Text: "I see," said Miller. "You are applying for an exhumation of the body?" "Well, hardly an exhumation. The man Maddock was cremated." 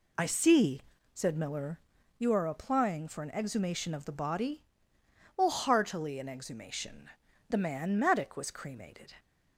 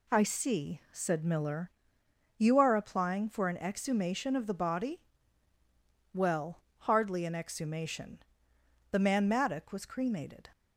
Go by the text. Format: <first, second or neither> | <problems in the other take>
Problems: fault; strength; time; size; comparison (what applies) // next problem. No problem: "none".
second | says "heartily" for "hardly"; at 5.4 s